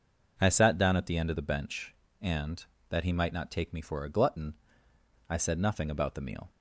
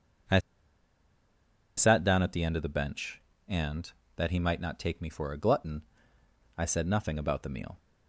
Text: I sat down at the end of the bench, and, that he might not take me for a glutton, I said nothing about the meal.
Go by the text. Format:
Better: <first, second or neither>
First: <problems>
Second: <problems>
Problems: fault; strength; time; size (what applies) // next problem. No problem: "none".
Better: first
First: none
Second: pauses between "I" and "sat"; strong; at 0.3 s; 1.3 s long